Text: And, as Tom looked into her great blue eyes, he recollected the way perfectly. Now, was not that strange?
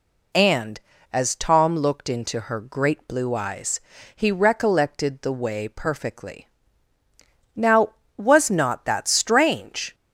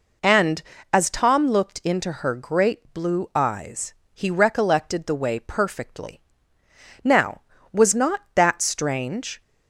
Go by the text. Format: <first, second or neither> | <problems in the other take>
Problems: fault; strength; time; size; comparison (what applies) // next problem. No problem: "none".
neither | none